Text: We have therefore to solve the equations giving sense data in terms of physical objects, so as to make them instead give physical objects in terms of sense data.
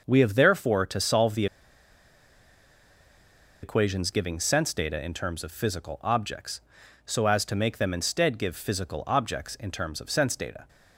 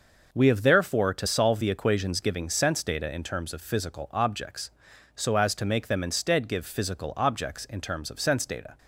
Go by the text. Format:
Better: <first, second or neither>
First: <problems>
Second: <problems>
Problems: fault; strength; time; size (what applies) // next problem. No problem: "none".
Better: second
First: pauses between "the" and "equations"; strong; at 1.4 s; 2.1 s long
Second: none